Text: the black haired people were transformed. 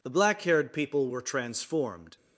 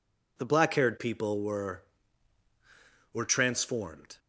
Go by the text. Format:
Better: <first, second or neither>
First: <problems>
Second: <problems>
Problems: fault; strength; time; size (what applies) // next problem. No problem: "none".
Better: first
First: none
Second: says "were" twice; at 3.1 s